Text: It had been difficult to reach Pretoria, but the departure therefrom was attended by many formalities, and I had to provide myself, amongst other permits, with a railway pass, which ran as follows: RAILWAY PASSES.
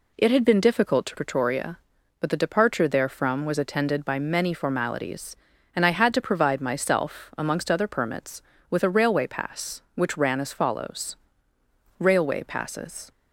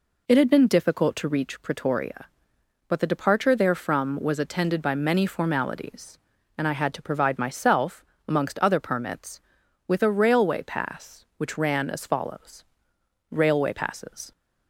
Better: second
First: skips "reach"; at 1.1 s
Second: none

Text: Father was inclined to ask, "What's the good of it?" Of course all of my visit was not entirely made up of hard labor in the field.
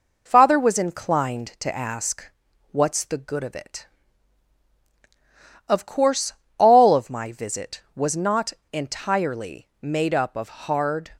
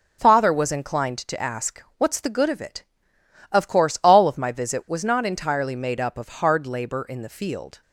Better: second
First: pauses between "course" and "all"; slight; at 6.3 s; 0.26 s long // pauses between "not" and "entirely"; slight; at 8.5 s; 0.19 s long // pauses between "entirely" and "made"; slight; at 9.6 s; 0.16 s long // stops before "labor in the field"; at 11.1 s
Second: none

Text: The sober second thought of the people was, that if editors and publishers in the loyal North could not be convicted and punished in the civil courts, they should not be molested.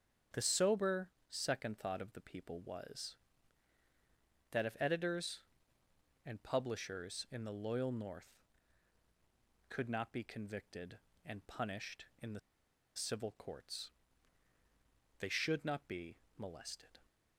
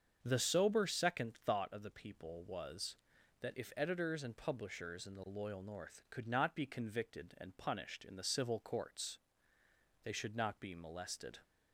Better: second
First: starts louder than the rest; strong; until 1.5 s; 7.5 dB // pauses between "sober" and "second"; slight; at 1.0 s; 0.22 s long // pauses between "the" and "civil"; noticeable; at 12.3 s; 0.56 s long // pauses between "be" and "molested"; slight; at 16.1 s; 0.20 s long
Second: starts louder than the rest; until 1.2 s; 7 dB

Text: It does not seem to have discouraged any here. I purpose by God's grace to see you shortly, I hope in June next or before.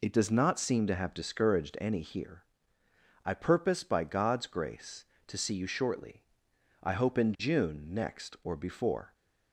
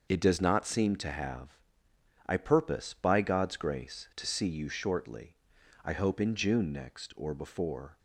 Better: first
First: none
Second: starts louder than the rest; noticeable; until 1.1 s; 6 dB // skips "discouraged any here"; at 1.9 s

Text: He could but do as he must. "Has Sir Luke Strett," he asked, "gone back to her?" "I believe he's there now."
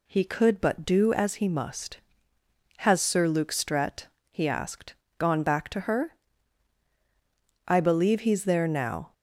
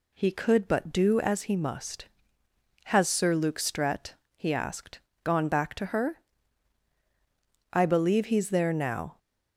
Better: neither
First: none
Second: none

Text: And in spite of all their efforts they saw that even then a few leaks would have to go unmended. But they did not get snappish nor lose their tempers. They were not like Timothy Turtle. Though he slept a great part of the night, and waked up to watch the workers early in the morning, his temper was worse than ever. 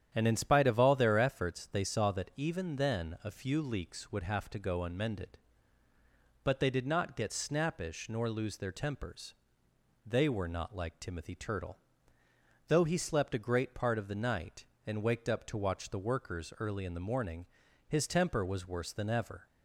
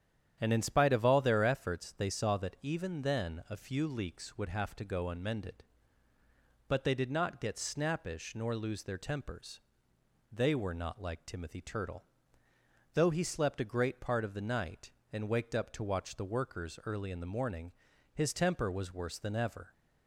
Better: neither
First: starts louder than the rest; strong; until 1.1 s; 9.5 dB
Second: starts louder than the rest; strong; until 1.4 s; 9.5 dB

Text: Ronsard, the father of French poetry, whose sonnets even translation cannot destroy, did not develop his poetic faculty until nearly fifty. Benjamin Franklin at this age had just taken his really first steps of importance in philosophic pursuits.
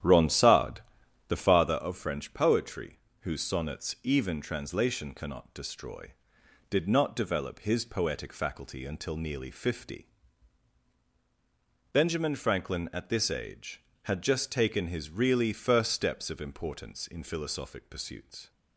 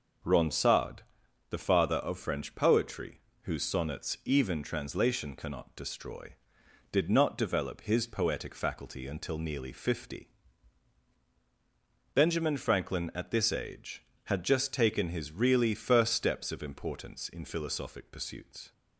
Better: second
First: starts louder than the rest; strong; until 1.8 s; 10.5 dB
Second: none

